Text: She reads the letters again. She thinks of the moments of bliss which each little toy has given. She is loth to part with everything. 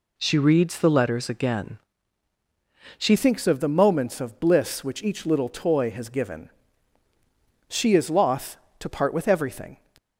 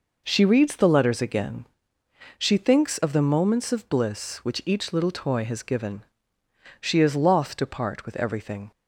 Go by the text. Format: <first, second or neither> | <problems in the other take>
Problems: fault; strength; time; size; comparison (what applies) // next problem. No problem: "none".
second | changes voice at "thinks"; from 3.1 s on; 6.6 s long